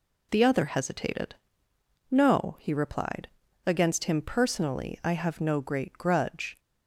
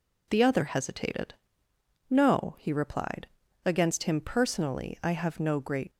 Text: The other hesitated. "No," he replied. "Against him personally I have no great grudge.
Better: first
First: none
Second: stops before "grudge"; at 5.9 s

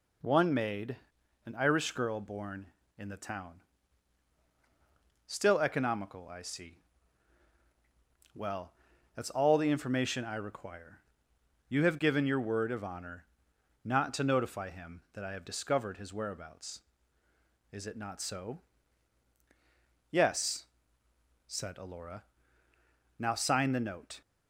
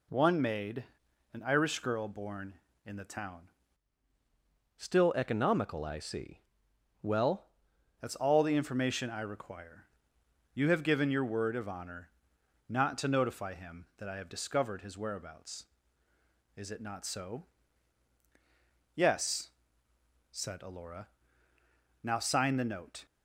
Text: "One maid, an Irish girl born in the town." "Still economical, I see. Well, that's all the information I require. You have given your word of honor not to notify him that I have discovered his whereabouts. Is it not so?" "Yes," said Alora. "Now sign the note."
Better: first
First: pauses between "honor" and "not"; noticeable; at 13.2 s; 0.56 s long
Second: changes voice from "Still" to "Well"; from 4.7 to 7.4 s; 2.7 s long // pauses between "honor" and "not"; noticeable; at 12.1 s; 0.56 s long

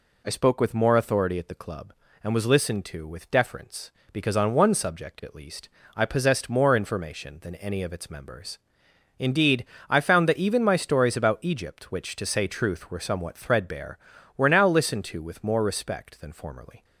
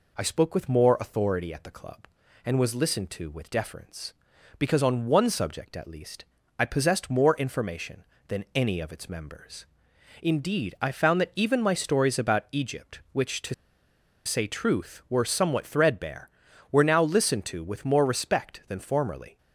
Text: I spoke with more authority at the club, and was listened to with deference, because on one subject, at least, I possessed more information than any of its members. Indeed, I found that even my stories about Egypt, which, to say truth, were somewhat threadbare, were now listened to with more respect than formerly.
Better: first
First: none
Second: pauses between "to" and "say"; noticeable; at 13.5 s; 0.71 s long

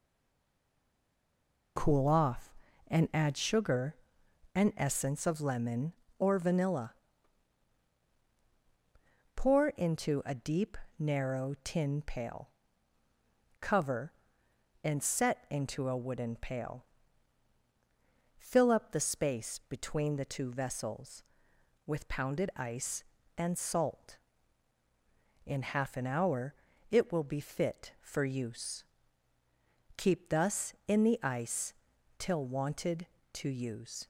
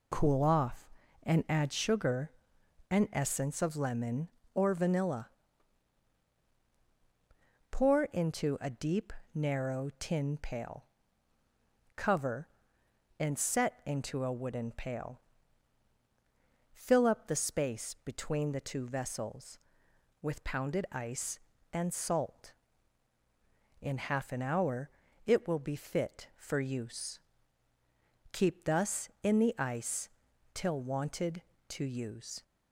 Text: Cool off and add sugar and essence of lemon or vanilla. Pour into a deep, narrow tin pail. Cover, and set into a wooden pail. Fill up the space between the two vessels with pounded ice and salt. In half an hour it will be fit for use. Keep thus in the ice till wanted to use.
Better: second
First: stays silent before the first word; noticeable; until 1.7 s; 1.7 s long // pauses between "hour" and "it"; slight; at 26.5 s; 0.34 s long // pauses between "ice" and "till"; noticeable; at 31.7 s; 0.46 s long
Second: pauses between "hour" and "it"; slight; at 24.9 s; 0.34 s long // pauses between "ice" and "till"; noticeable; at 30.0 s; 0.46 s long

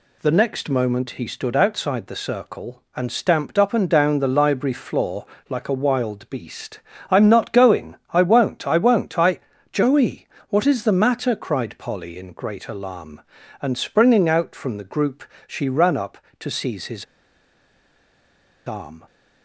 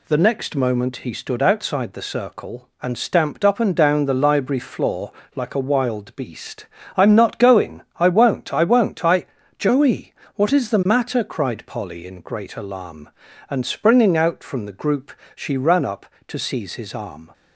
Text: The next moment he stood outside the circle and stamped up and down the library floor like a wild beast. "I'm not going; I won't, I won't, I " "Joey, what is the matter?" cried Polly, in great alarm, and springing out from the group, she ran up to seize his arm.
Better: second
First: pauses between "floor" and "like"; slight; at 5.2 s; 0.24 s long // pauses between "his" and "arm"; strong; at 17.0 s; 1.6 s long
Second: pauses between "floor" and "like"; slight; at 5.1 s; 0.24 s long

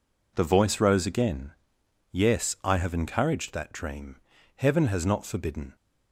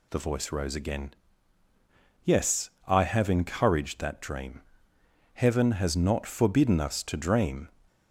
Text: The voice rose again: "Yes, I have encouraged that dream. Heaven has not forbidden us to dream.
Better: second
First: stops before "us to dream"; at 5.7 s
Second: none

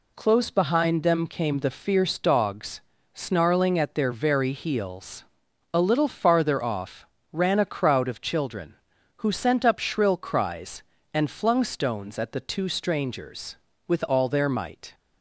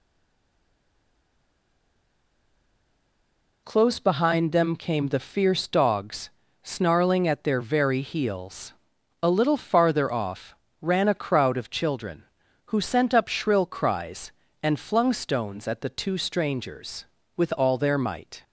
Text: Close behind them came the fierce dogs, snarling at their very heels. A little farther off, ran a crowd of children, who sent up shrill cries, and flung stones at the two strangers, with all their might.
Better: first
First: none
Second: stays silent before the first word; strong; until 3.6 s; 3.6 s long

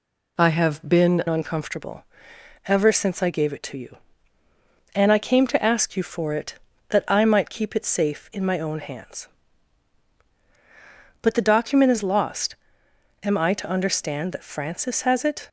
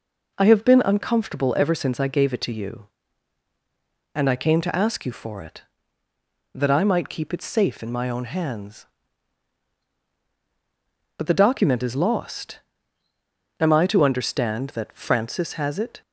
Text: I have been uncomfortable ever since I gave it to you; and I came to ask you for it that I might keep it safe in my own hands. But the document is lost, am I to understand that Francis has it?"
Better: second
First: changes voice at "uncomfortable"; from 1.2 s on; 14.2 s long // pauses between "uncomfortable" and "ever"; noticeable; at 2.0 s; 0.62 s long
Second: none

